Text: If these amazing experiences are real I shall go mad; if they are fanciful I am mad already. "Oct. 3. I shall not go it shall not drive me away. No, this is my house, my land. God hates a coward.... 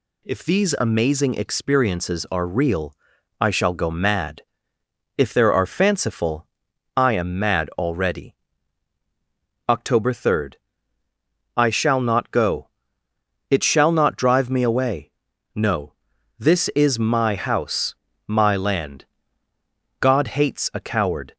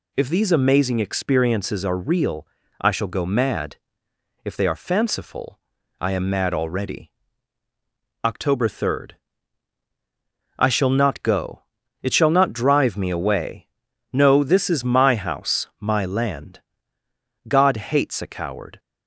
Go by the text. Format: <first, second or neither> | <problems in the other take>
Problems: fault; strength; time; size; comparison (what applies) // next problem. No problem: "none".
second | pauses between "real" and "I"; at 2.9 s; 0.44 s long; slight in the second // says "there" for "they"; at 5.3 s // pauses between "fanciful" and "I"; noticeable; at 6.4 s; 0.50 s long; also in the second // pauses between "go" and "it"; noticeable; at 12.6 s; 0.82 s long; also in the second